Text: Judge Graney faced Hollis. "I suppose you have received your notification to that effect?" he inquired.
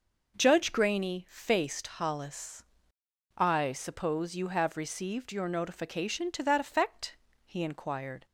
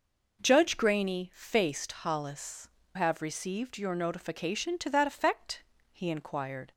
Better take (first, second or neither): first